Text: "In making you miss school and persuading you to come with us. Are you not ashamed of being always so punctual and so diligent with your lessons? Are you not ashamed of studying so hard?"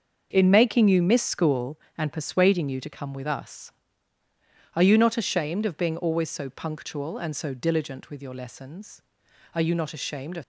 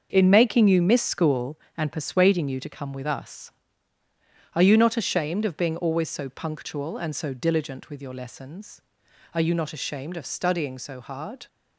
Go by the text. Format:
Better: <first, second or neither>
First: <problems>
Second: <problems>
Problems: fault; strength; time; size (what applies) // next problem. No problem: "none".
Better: second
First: starts louder than the rest; until 1.3 s; 6.5 dB // stops before "studying so hard"; at 10.4 s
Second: starts louder than the rest; until 1.1 s; 6.5 dB